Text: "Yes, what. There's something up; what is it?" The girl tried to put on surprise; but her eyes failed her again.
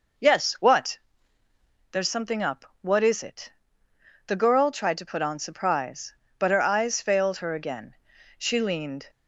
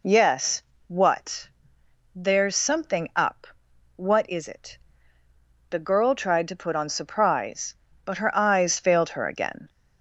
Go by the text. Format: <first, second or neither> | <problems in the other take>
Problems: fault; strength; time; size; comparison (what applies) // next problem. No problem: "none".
second | goes on to say "She leaned"; noticeable; from 8.3 s on; 0.72 s long